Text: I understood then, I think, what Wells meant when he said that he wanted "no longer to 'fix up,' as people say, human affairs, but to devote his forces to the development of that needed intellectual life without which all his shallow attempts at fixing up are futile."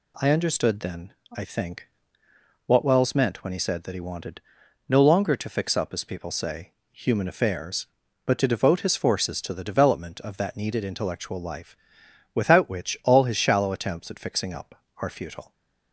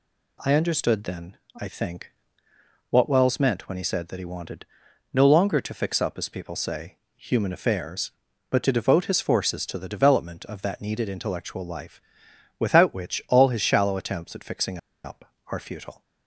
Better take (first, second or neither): first